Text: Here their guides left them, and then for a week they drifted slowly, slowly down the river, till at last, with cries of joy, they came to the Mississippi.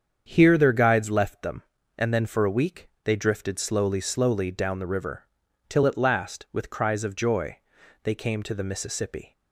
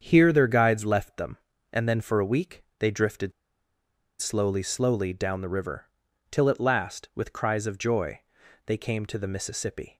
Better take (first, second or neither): first